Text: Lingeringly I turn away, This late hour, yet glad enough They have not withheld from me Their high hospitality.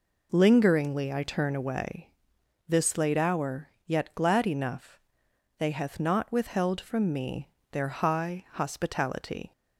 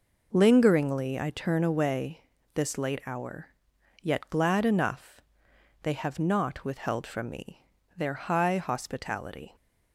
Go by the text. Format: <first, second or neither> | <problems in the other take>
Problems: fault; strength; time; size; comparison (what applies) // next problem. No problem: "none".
second | pauses between "enough" and "They"; noticeable; at 4.9 s; 0.58 s long; noticeable in the second // says "hath" for "have"; at 5.7 s // pauses between "me" and "Their"; slight; at 7.4 s; 0.22 s long; slight in the second